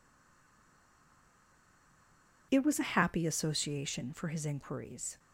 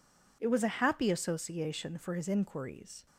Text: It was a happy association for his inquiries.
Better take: second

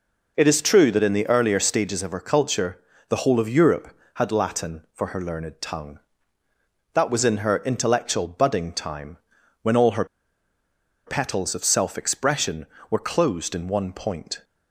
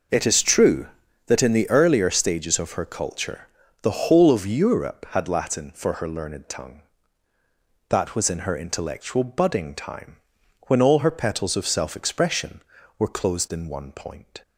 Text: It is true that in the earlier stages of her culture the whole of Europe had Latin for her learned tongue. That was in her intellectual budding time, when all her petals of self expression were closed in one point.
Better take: second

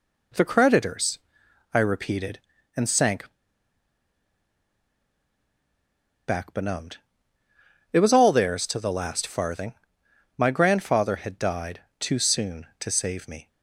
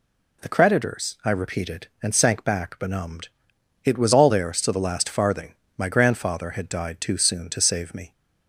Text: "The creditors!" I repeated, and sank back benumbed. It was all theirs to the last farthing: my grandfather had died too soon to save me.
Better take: second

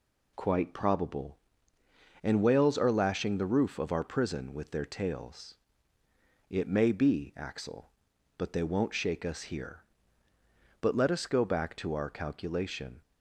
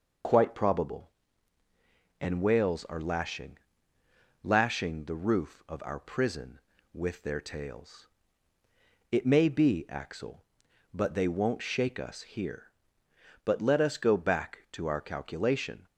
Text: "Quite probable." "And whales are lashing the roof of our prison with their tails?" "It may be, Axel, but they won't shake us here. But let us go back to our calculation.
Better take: first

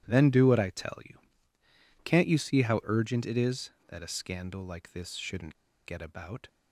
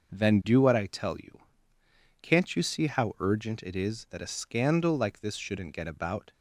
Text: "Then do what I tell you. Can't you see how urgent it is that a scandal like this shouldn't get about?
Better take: second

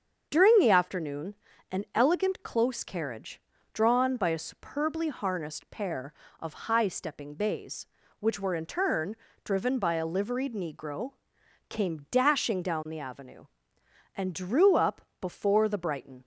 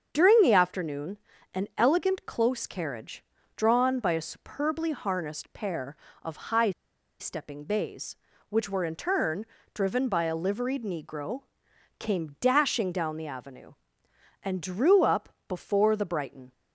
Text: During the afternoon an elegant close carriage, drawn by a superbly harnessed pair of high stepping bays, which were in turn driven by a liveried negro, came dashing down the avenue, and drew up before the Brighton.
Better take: first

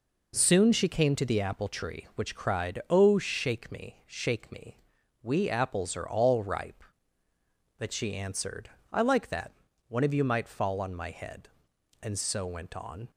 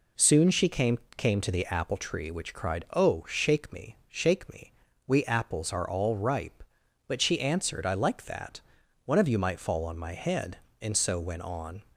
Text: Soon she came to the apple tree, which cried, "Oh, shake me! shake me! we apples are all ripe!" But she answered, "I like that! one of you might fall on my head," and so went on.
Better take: first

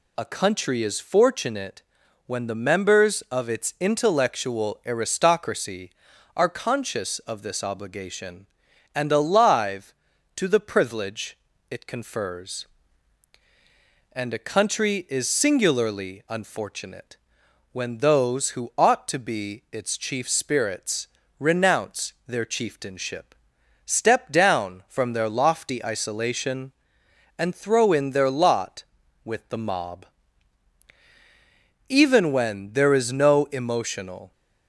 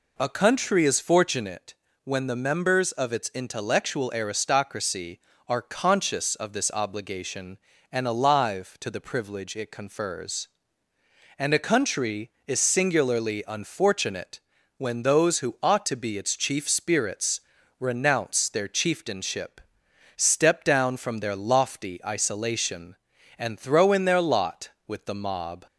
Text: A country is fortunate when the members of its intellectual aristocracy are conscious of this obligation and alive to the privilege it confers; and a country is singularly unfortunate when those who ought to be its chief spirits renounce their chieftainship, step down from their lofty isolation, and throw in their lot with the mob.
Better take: second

